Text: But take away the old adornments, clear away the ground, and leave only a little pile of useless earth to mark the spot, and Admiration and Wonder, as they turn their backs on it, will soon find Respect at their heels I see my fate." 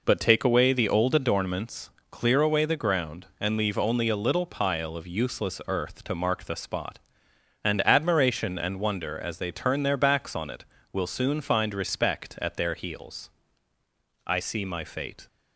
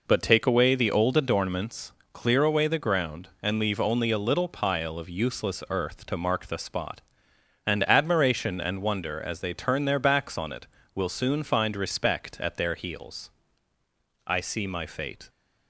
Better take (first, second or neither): neither